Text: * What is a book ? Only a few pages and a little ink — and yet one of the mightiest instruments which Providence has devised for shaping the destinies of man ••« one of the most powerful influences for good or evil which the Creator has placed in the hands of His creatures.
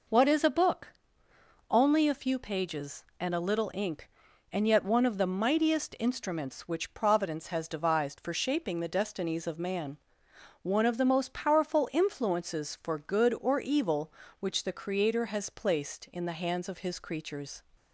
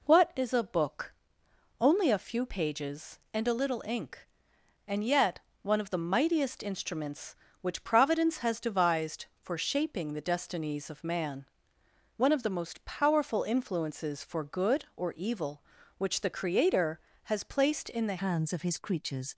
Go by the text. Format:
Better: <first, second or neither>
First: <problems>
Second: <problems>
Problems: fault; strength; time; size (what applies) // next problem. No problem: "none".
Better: first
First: none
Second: pauses between "yet" and "one"; slight; at 5.3 s; 0.24 s long // changes voice at "hands"; from 18.1 s on; 1.2 s long